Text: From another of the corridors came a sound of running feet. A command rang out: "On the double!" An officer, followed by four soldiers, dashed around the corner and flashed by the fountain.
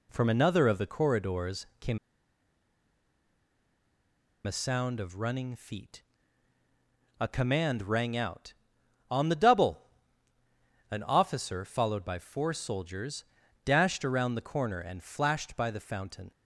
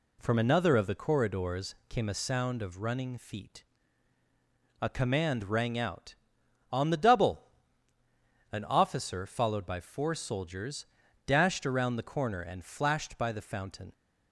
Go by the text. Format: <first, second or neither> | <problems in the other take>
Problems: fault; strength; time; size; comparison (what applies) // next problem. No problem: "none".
second | pauses between "came" and "a"; strong; at 1.9 s; 2.4 s long